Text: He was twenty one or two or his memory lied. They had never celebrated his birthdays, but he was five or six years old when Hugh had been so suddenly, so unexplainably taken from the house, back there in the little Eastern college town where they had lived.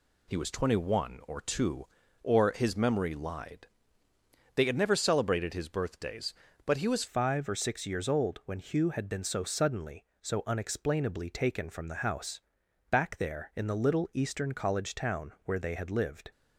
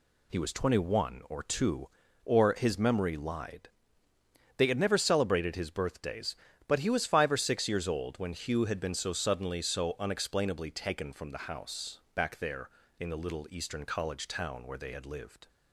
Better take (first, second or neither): second